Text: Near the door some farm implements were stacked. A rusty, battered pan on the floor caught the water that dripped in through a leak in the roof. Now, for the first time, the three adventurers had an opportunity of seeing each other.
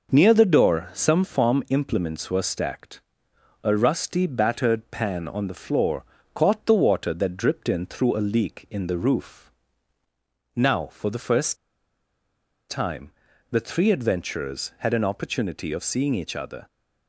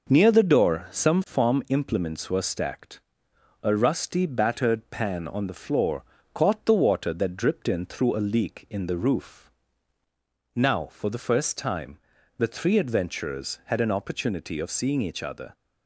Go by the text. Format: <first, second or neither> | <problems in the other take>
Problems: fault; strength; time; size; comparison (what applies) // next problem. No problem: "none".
second | pauses between "floor" and "caught"; slight; at 6.0 s; 0.30 s long; slight in the second // pauses between "first" and "time"; at 11.5 s; 1.1 s long